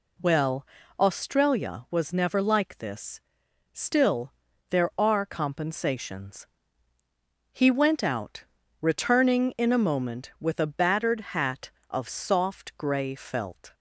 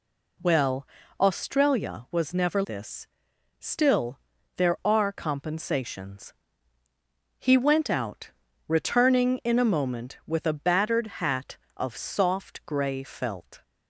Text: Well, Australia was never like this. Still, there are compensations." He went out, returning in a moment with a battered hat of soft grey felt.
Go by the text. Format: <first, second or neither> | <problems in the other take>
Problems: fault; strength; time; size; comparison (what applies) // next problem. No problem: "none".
first | skips "like"; at 2.6 s // pauses between "battered" and "hat"; slight; at 11.0 s; 0.16 s long; slight in the first